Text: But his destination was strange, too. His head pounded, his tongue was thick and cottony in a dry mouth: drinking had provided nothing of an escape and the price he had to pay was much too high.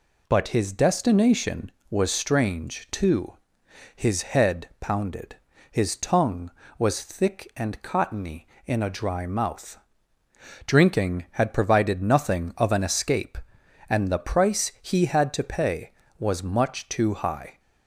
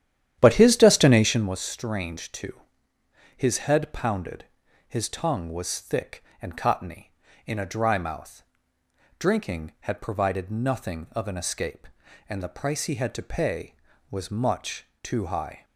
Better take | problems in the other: first | starts louder than the rest; strong; until 1.6 s; 11 dB // pauses between "much" and "too"; slight; at 14.8 s; 0.16 s long

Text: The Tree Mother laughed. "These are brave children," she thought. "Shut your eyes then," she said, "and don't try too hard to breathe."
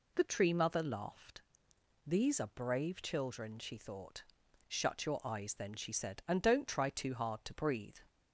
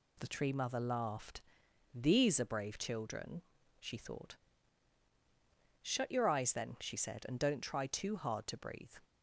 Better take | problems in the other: neither | none

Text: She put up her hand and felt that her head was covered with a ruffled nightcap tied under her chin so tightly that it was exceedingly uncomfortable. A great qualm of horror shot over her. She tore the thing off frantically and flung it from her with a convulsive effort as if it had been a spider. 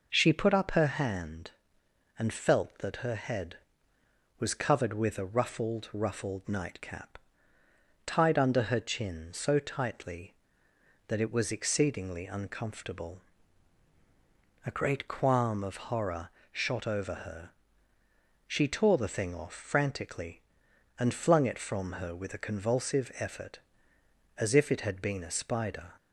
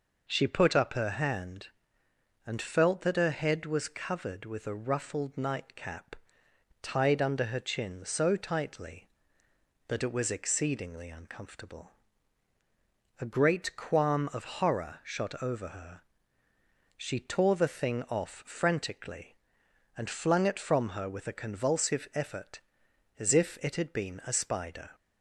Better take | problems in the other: second | says "ruffled" twice; at 5.9 s // pauses between "nightcap" and "tied"; noticeable; at 7.1 s; 0.90 s long; noticeable in the second // pauses between "horror" and "shot"; slight; at 16.3 s; 0.20 s long

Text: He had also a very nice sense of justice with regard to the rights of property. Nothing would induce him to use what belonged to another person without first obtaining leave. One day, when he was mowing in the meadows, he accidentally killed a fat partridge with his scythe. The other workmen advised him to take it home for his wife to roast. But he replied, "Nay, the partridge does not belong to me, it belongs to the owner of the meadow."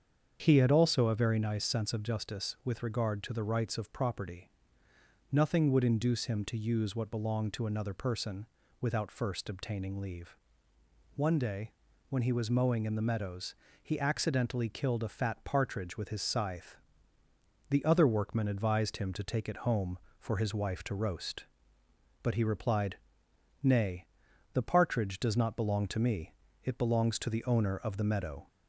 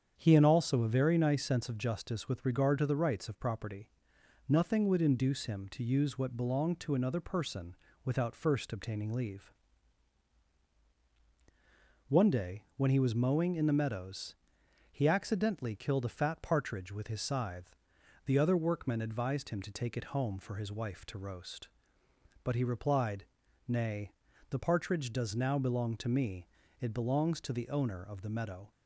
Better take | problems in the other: first | starts louder than the rest; strong; until 1.1 s; 8 dB; strong in the first // pauses between "person" and "without"; slight; at 7.7 s; 0.28 s long; slight in the first // says "now" for "not"; at 25.3 s

